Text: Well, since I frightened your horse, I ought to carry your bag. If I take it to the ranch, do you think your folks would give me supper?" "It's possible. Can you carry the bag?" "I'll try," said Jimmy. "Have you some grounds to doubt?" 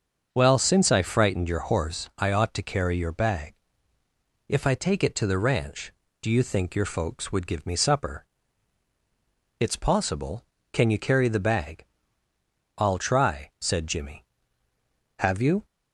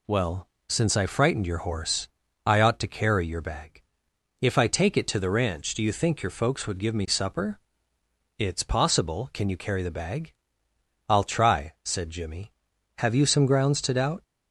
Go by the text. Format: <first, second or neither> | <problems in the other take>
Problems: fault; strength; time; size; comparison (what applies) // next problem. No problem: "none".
second | starts louder than the rest; until 1.3 s; 6.5 dB // stops before "some grounds to doubt"; at 15.6 s